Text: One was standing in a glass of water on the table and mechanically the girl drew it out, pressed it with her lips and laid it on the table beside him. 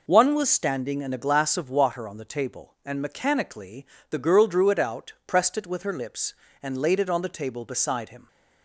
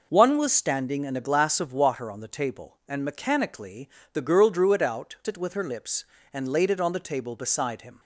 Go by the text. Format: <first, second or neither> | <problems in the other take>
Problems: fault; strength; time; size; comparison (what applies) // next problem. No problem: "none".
first | pauses between "mechanically" and "the"; slight; at 3.8 s; 0.24 s long; slight in the first // skips "pressed"; at 5.2 s